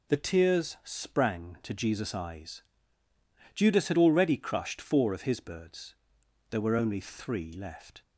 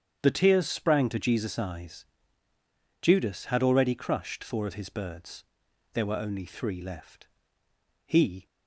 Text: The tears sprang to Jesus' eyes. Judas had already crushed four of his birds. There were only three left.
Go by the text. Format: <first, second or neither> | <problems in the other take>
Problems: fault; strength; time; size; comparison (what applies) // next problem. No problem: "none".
first | starts louder than the rest; strong; until 1.2 s; 8.5 dB // goes on to say "He"; slight; from 8.0 s on; 0.40 s long